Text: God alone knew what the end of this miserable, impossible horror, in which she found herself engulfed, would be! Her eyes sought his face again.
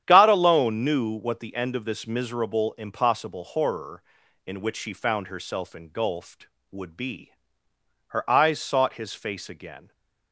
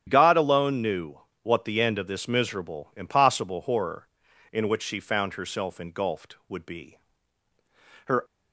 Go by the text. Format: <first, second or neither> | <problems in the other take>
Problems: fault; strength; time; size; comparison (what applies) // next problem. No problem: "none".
first | starts louder than the rest; strong; until 1.0 s; 9.5 dB; strong in the first // pauses between "knew" and "what"; slight; at 1.1 s; 0.24 s long // stops before "eyes sought his face again"; at 8.2 s